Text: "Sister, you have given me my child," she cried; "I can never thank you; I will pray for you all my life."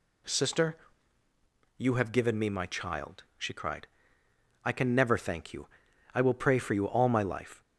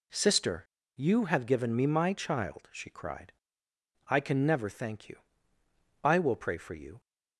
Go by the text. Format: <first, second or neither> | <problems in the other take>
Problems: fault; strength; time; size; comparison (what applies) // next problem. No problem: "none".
first | stops before "all my life"; at 6.9 s